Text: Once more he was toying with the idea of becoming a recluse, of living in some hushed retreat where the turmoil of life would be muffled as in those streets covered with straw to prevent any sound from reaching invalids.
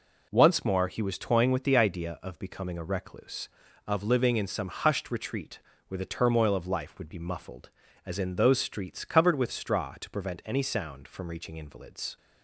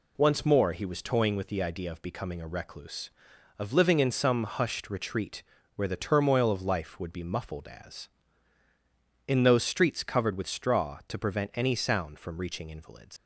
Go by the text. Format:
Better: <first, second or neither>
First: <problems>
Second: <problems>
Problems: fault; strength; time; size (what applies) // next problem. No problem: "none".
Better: first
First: pauses between "retreat" and "where"; slight; at 5.6 s; 0.26 s long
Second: pauses between "retreat" and "where"; slight; at 5.4 s; 0.34 s long // leaves "invalids" unfinished; at 13.1 s; 105 ms